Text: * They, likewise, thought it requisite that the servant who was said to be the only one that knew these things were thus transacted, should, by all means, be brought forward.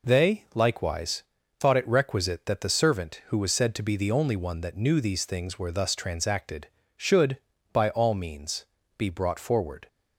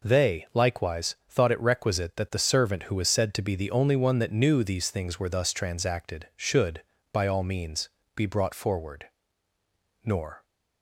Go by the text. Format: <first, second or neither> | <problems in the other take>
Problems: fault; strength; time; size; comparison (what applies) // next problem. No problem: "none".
first | goes on to say "Nor"; slight; from 10.0 s on; 0.40 s long